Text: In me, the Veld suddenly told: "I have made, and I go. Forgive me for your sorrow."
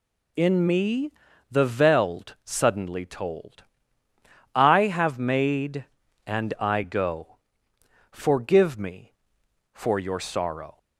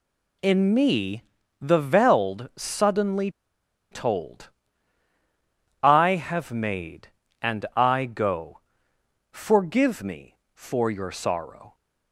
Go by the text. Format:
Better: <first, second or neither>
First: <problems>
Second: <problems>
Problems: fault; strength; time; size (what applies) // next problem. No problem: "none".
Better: first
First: none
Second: pauses between "suddenly" and "told"; noticeable; at 3.2 s; 0.62 s long